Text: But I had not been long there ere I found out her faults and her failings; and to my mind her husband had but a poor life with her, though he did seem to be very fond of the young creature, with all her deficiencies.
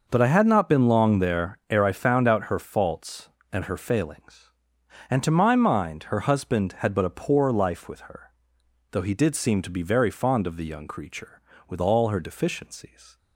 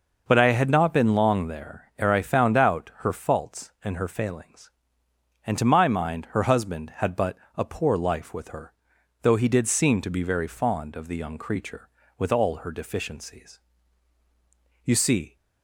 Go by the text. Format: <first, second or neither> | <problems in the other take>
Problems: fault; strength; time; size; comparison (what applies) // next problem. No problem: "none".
first | pauses between "but" and "a"; slight; at 7.3 s; 0.20 s long // goes on to say "You see"; from 14.8 s on; 0.52 s long